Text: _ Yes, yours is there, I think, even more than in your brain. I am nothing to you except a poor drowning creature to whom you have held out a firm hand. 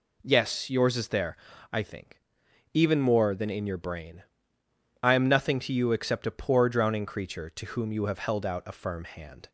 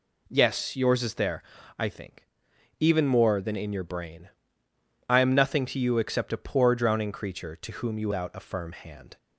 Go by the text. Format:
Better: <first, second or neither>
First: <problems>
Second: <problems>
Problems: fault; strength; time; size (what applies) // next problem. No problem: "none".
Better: first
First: none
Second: skips "have held"; at 8.1 s